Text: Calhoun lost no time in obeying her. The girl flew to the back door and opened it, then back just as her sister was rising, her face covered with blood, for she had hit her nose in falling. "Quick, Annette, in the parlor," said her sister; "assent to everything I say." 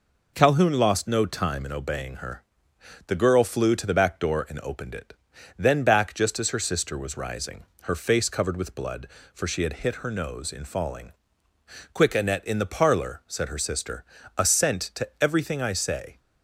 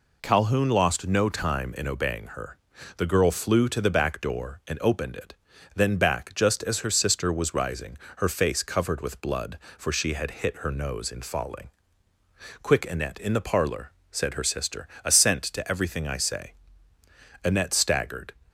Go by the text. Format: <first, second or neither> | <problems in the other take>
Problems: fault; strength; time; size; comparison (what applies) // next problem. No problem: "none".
first | goes on to say "Annette staggered"; noticeable; from 17.4 s on; 0.90 s long